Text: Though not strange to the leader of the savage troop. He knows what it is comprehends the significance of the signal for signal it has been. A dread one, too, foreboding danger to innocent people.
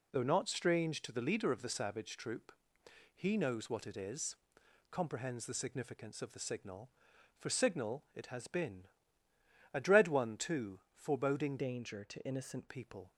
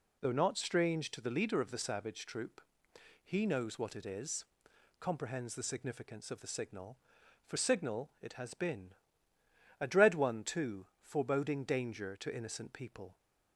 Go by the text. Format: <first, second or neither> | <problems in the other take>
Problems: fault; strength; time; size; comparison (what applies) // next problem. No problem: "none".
second | pauses between "is" and "comprehends"; noticeable; at 4.3 s; 0.54 s long; noticeable in the second // changes voice from "danger" to "innocent"; from 11.5 to 12.6 s; 1.1 s long